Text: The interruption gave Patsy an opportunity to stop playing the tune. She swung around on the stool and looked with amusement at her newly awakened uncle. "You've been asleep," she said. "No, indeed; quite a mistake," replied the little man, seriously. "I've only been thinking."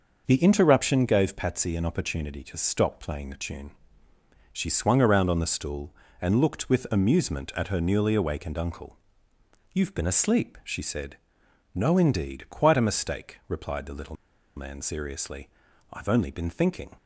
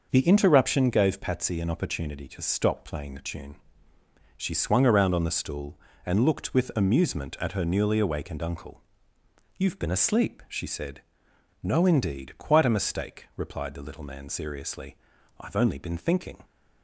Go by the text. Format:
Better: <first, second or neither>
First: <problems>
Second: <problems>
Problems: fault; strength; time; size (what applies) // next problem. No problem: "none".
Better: second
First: starts louder than the rest; noticeable; until 1.2 s; 6 dB // pauses between "little" and "man"; at 14.1 s; 0.41 s long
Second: starts louder than the rest; noticeable; until 1.1 s; 6 dB